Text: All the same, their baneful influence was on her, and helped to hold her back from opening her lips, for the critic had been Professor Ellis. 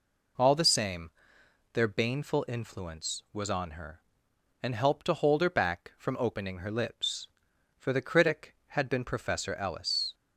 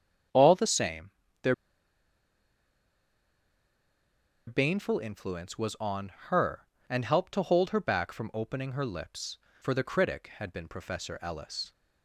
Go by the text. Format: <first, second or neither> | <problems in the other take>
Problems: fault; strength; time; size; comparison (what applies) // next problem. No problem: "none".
first | starts louder than the rest; strong; until 4.5 s; 8 dB // pauses between "their" and "baneful"; strong; at 1.5 s; 2.9 s long // pauses between "on" and "her"; slight; at 6.1 s; 0.16 s long